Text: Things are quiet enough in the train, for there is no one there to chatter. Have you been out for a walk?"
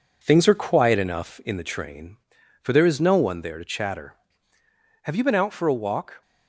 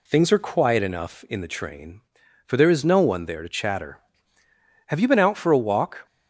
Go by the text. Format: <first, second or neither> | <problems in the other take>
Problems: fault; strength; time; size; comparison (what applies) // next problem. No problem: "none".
second | gets quieter; noticeable; throughout; 4 dB